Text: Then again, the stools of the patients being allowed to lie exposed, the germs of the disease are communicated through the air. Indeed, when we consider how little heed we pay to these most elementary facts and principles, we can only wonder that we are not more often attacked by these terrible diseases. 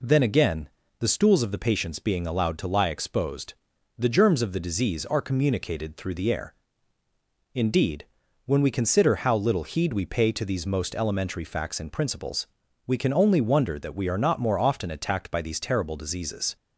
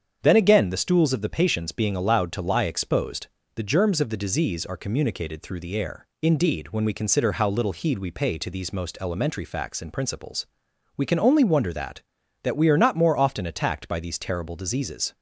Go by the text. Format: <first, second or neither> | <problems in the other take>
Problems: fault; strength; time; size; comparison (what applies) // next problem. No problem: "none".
first | starts louder than the rest; strong; until 1.2 s; 7.5 dB // says "that" twice; at 12.4 s